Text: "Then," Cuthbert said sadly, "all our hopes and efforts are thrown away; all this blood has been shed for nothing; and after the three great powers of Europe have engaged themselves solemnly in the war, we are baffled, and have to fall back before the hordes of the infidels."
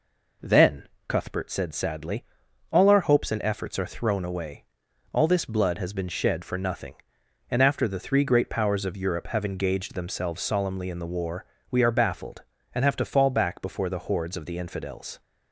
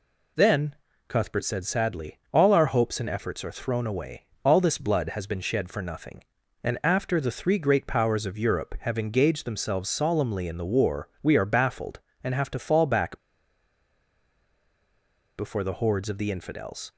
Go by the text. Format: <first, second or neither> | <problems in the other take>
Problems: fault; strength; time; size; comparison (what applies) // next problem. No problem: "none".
first | pauses between "back" and "before"; strong; at 13.1 s; 2.1 s long